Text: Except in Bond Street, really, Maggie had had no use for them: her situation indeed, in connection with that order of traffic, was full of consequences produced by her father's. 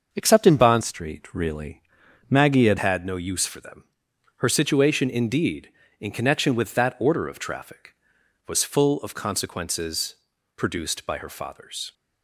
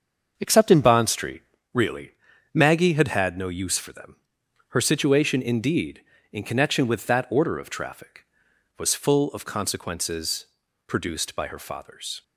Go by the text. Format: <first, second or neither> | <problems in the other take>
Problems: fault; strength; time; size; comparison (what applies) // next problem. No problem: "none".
second | starts louder than the rest; until 1.1 s; 6.5 dB; also in the second // changes voice from "Street" to "had"; from 0.8 to 2.7 s; 1.9 s long // pauses between "consequences" and "produced"; at 10.1 s; 0.42 s long; also in the second